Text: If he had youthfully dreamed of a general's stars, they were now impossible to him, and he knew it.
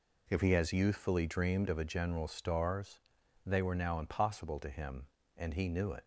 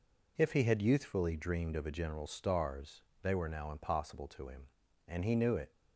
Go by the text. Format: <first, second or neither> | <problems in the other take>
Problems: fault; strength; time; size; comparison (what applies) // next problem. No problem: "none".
second | says "has" for "had"; at 0.5 s